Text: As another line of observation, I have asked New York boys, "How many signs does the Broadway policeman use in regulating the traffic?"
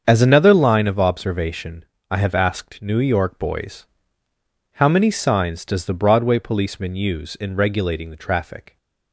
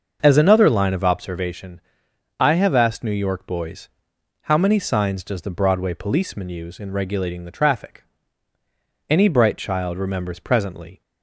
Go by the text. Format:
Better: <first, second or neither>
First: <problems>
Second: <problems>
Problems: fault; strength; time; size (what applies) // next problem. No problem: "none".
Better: first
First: starts louder than the rest; strong; until 1.0 s; 7 dB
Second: starts louder than the rest; until 1.2 s; 6.5 dB // goes on to say "Any bright child remembers presently"; strong; from 9.0 s on; 1.9 s long